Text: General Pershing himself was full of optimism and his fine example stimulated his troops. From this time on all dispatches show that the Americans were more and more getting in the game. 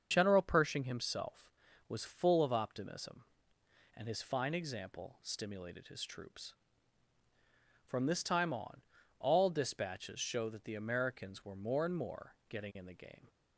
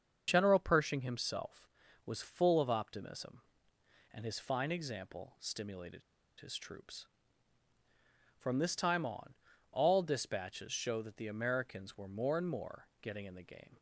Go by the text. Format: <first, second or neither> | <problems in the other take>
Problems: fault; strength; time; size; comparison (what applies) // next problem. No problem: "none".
first | starts louder than the rest; until 1.2 s; 6.5 dB; also in the first // pauses between "stimulated" and "his"; at 6.0 s; 0.38 s long // pauses between "on" and "all"; at 9.3 s; 0.38 s long; also in the first // pauses between "more" and "getting"; slight; at 12.8 s; 0.16 s long; slight in the first